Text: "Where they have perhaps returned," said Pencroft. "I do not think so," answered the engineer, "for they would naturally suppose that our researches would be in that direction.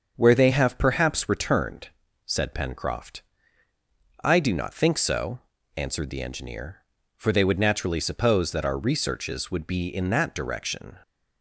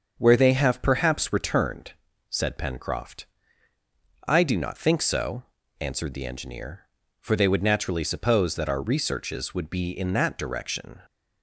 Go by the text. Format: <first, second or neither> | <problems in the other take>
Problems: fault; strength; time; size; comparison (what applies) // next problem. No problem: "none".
neither | starts louder than the rest; the same in both